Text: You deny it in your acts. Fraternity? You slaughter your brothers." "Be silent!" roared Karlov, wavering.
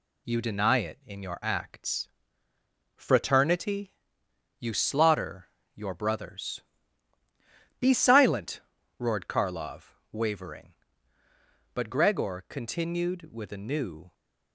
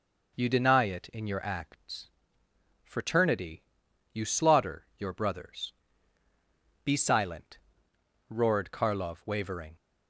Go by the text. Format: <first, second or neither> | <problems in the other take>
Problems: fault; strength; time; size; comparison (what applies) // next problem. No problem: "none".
second | pauses between "slaughter" and "your"; slight; at 5.4 s; 0.26 s long // goes on to say "But Gregor continued with a new"; strong; from 11.7 s on; 2.3 s long